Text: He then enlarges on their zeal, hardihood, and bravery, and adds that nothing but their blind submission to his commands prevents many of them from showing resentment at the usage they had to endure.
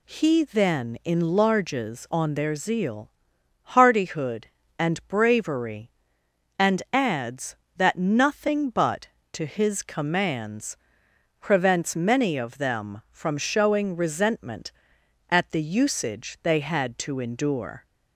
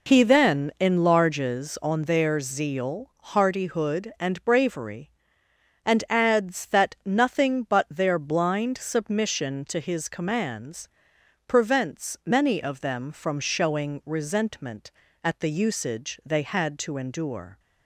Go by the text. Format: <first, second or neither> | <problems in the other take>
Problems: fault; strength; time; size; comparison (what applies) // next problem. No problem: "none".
second | skips "their blind submission"; at 9.2 s // pauses between "commands" and "prevents"; noticeable; at 10.7 s; 0.64 s long; noticeable in the second